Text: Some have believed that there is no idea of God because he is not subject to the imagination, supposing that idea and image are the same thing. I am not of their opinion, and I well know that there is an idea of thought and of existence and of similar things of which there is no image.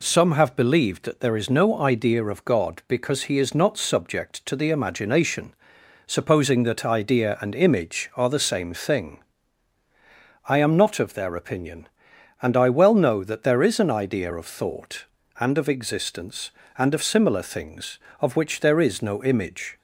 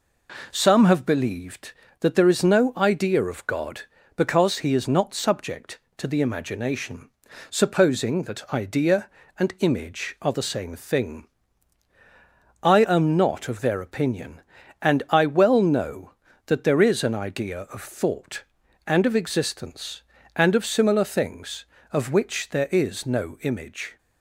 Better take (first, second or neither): neither